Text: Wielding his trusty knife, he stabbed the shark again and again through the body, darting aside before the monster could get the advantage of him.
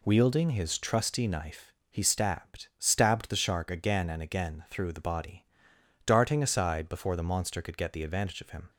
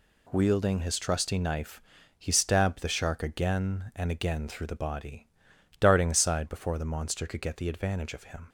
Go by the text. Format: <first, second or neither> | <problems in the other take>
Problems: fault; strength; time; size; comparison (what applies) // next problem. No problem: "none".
second | says "stabbed" twice; at 2.7 s